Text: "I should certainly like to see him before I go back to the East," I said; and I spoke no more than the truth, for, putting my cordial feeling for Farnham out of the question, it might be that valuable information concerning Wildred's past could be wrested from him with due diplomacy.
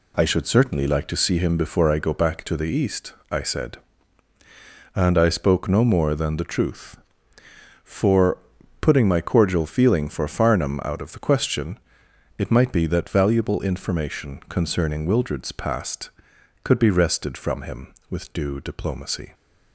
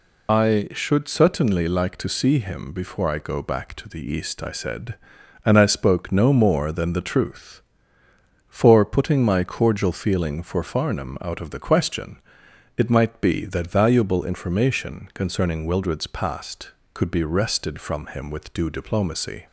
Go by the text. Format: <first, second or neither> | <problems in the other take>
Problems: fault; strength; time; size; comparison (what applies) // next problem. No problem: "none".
first | loses the start of "I"; at 0.2 s; 75 ms